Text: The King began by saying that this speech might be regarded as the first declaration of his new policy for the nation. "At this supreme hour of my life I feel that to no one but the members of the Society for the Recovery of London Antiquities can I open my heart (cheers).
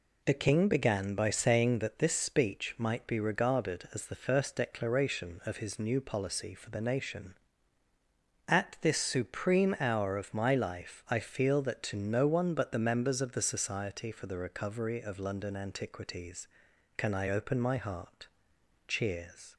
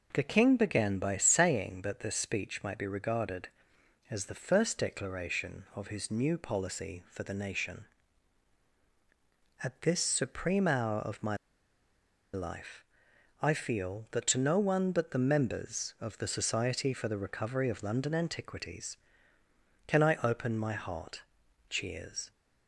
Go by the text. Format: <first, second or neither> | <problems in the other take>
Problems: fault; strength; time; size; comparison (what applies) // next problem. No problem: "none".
first | pauses between "my" and "life"; noticeable; at 11.3 s; 0.96 s long // pauses between "life" and "I"; noticeable; at 12.8 s; 0.58 s long